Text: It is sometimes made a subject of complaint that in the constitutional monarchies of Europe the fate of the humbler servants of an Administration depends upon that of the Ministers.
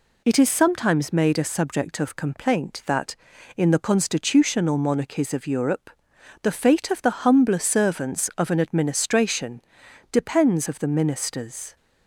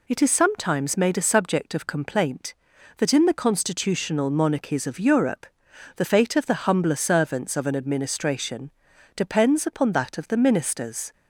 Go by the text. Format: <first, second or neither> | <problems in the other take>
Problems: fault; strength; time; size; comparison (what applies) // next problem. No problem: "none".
second | pauses between "Europe" and "the"; noticeable; at 5.9 s; 0.52 s long; noticeable in the second // pauses between "Administration" and "depends"; noticeable; at 9.6 s; 0.50 s long; also in the second // skips "upon that"; at 10.6 s